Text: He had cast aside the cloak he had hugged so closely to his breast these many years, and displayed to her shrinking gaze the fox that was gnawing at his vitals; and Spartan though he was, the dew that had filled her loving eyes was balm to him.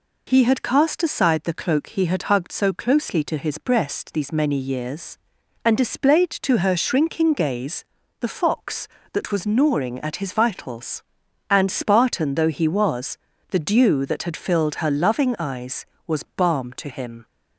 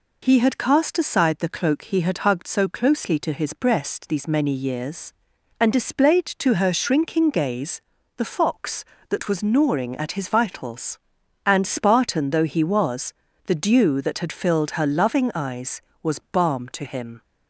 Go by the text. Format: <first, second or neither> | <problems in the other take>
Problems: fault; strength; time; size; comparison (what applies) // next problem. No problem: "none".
neither | pauses between "gaze" and "the"; slight; the same in both